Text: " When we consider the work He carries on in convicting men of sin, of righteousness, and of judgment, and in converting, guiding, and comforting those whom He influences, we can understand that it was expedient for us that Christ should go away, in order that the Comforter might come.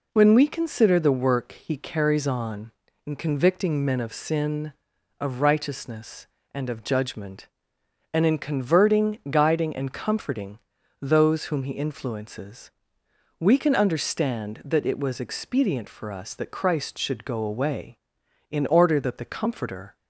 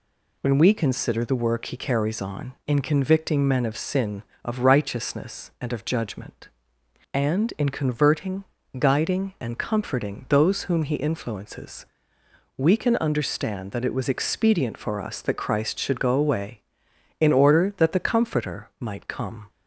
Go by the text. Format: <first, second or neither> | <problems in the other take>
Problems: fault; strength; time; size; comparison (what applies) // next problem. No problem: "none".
second | pauses between "comforting" and "those"; at 10.5 s; 0.42 s long // stops before "might come"; at 19.9 s